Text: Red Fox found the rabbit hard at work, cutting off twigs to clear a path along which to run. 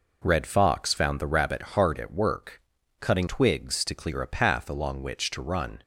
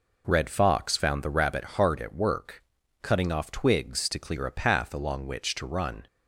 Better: second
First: skips "off"; at 3.2 s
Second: none

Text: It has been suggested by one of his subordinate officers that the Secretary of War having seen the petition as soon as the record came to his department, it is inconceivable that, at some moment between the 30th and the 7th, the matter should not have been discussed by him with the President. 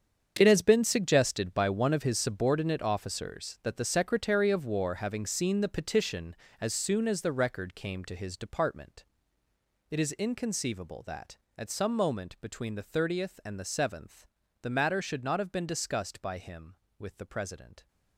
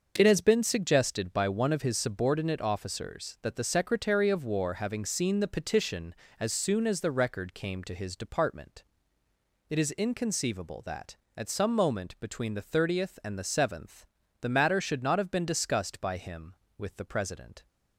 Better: second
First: gets quieter; strong; throughout; 13.5 dB // starts louder than the rest; strong; until 1.3 s; 7.5 dB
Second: starts louder than the rest; until 1.1 s; 6 dB

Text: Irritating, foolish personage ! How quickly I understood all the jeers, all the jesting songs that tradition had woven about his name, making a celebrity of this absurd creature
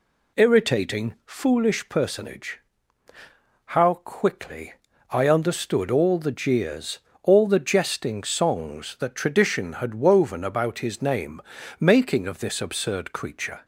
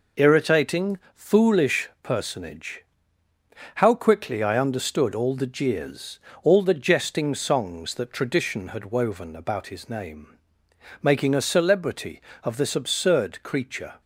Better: second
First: pauses between "quickly" and "I"; at 4.7 s; 0.38 s long // skips "a celebrity"; at 12.2 s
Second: none

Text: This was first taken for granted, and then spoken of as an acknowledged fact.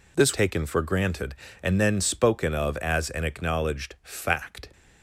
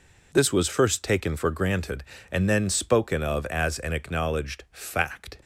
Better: second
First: skips "was first"; at 0.3 s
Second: none

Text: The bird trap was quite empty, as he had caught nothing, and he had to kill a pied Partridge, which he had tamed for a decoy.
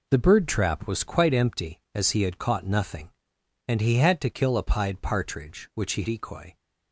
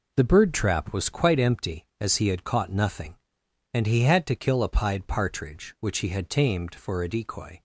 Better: second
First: skips "had tamed for a"; at 6.0 s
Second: none

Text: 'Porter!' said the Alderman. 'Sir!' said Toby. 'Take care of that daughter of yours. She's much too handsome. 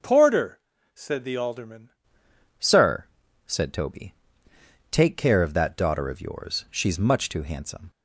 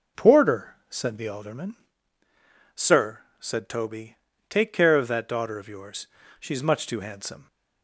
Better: second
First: changes voice at "Sir"; from 2.6 s on; 5.3 s long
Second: none

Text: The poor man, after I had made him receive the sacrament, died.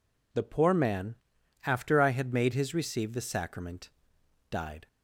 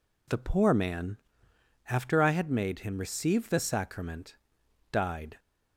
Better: second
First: says "his" for "him"; at 2.5 s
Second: none

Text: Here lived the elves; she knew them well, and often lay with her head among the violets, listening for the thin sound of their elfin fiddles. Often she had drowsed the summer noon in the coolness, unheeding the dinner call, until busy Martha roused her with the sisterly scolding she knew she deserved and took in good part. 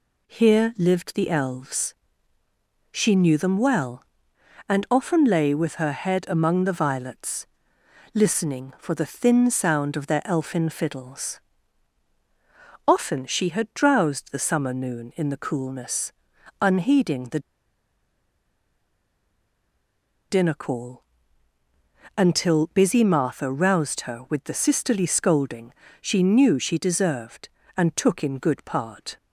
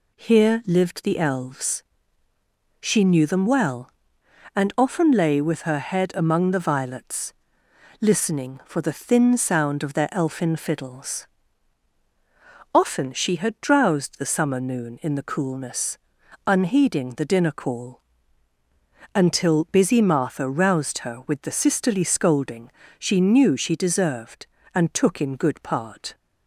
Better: second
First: pauses between "the" and "dinner"; strong; at 17.3 s; 2.9 s long // pauses between "scolding" and "she"; slight; at 25.7 s; 0.28 s long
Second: pauses between "scolding" and "she"; slight; at 22.7 s; 0.28 s long

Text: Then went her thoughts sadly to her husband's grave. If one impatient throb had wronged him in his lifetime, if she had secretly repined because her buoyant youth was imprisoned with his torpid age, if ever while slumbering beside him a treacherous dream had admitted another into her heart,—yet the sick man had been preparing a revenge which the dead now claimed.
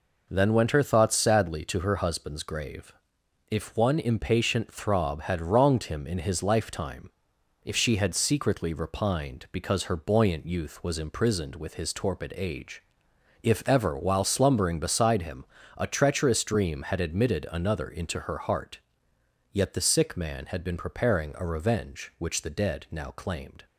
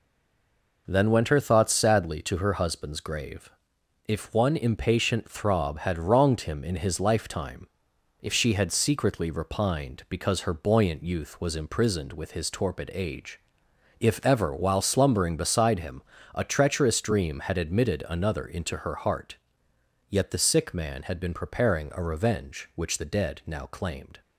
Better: first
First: pauses between "him" and "a"; slight; at 15.4 s; 0.34 s long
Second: stays silent before the first word; slight; until 0.8 s; 0.8 s long // pauses between "him" and "a"; slight; at 16.0 s; 0.34 s long

